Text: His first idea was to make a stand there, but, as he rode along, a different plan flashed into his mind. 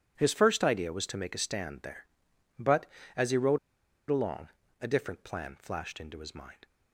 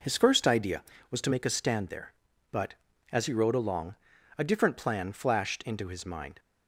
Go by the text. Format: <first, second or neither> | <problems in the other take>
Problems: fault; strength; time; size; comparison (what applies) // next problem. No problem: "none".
second | pauses between "rode" and "along"; noticeable; at 3.5 s; 0.52 s long